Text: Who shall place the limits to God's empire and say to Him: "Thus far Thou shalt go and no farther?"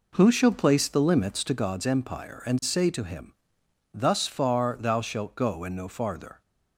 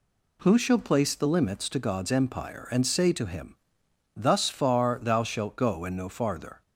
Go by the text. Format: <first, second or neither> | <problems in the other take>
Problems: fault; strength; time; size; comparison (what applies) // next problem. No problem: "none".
second | starts louder than the rest; noticeable; until 1.8 s; 4 dB